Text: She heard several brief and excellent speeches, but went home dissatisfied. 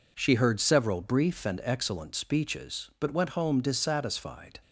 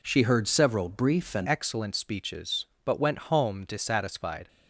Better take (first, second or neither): first